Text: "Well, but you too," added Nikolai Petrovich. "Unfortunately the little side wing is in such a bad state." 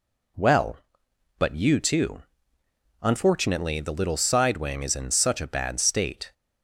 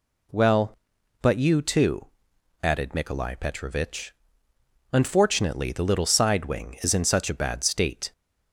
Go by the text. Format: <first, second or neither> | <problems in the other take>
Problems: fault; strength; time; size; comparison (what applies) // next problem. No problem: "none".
second | skips "added Nikolai Petrovich"; at 2.6 s